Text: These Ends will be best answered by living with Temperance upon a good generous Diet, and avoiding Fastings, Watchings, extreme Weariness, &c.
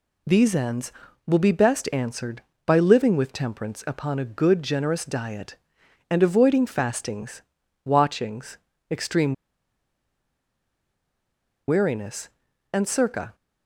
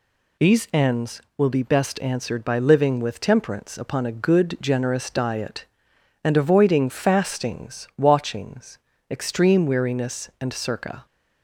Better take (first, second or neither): second